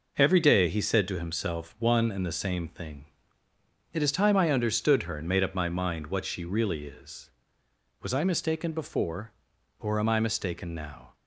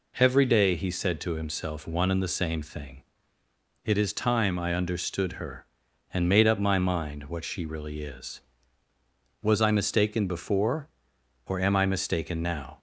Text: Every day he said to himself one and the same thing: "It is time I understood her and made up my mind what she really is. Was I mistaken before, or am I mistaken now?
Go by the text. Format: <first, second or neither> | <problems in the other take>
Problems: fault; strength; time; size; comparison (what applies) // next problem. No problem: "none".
neither | none